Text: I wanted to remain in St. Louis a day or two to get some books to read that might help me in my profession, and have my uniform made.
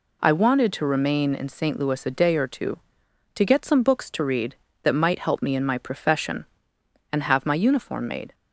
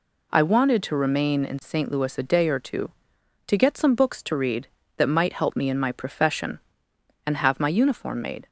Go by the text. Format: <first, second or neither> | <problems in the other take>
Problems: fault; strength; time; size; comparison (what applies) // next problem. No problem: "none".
neither | none